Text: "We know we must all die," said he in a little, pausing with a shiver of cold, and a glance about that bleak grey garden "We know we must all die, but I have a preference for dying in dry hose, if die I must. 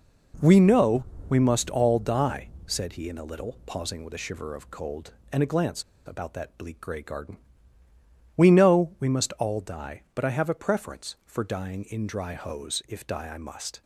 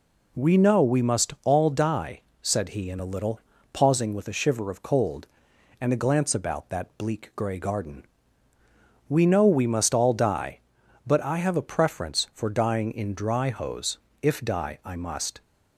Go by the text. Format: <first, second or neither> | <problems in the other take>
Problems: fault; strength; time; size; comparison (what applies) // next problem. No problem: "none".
second | pauses between "know" and "we"; slight; at 1.0 s; 0.24 s long // pauses between "glance" and "about"; slight; at 5.8 s; 0.24 s long // pauses between "garden" and "We"; noticeable; at 7.3 s; 0.98 s long; also in the second